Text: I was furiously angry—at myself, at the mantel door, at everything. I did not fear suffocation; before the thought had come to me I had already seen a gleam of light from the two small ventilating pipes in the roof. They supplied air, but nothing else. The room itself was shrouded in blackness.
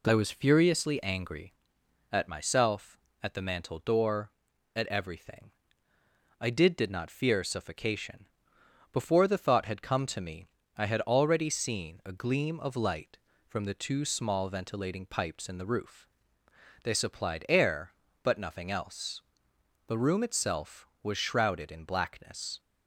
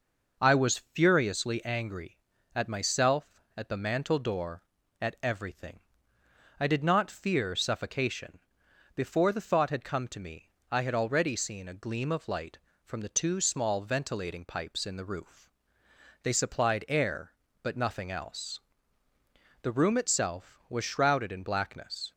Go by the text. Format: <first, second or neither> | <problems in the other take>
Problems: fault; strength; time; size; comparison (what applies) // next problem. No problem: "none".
second | says "did" twice; at 6.7 s // pauses between "me" and "I"; slight; at 10.4 s; 0.32 s long; slight in the second